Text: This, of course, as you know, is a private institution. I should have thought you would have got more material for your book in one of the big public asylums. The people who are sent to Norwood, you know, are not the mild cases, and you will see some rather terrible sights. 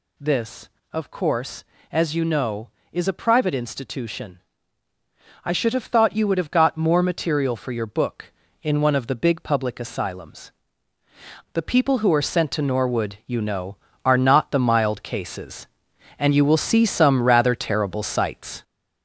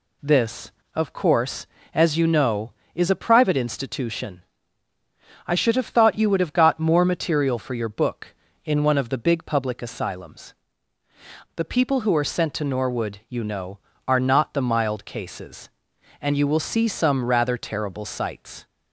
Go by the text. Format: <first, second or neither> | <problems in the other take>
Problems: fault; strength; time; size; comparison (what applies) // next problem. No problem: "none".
second | gets louder; noticeable; throughout; 5 dB